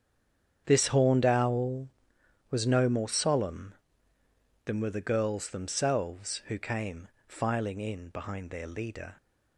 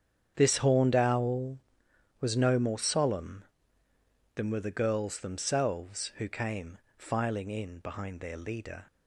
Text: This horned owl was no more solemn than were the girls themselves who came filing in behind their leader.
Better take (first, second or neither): second